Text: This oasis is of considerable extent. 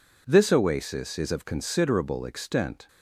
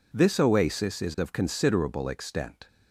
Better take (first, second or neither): neither